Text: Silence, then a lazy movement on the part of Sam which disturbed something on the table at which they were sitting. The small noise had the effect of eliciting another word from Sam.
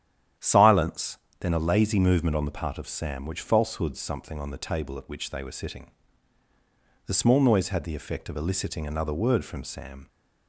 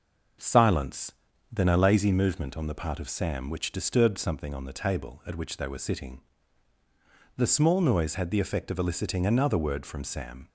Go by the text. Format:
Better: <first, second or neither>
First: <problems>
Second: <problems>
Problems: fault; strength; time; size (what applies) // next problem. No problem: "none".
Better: second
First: starts louder than the rest; strong; until 1.6 s; 10 dB // says "falsehoods" for "disturbed"; at 3.4 s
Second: starts louder than the rest; until 1.8 s; 6.5 dB